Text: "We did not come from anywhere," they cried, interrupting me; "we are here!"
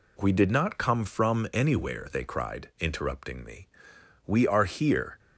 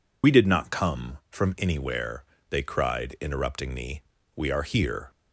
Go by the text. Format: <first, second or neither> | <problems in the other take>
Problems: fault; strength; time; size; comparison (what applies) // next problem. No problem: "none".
first | loses the start of "We"; at 0.2 s; 55 ms